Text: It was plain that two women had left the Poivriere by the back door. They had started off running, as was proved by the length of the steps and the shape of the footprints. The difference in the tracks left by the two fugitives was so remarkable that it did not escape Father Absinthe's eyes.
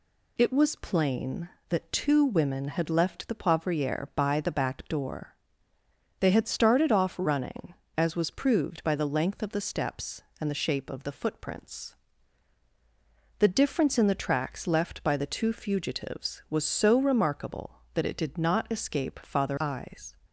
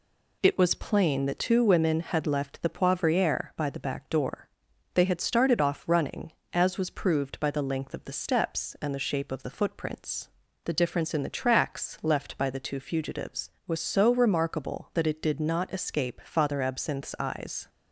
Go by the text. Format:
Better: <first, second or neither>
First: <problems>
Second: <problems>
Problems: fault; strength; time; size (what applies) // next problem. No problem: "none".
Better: second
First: skips "Absinthe's"; at 19.5 s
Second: none